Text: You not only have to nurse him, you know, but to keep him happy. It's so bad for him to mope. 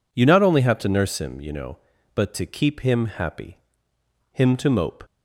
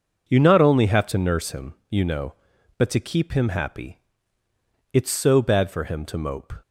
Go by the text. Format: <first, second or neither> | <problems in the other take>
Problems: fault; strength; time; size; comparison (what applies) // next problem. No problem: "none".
second | skips "It's so bad for"; at 3.9 s